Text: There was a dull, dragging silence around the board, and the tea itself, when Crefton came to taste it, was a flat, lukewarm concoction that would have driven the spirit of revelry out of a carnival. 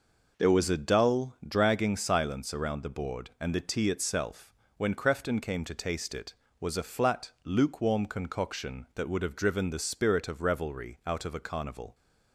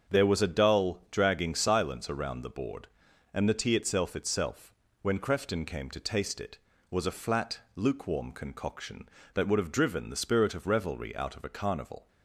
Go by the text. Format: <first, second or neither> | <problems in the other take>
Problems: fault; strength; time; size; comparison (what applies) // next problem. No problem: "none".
first | starts louder than the rest; until 1.2 s; 7 dB // says "itself" twice; at 4.1 s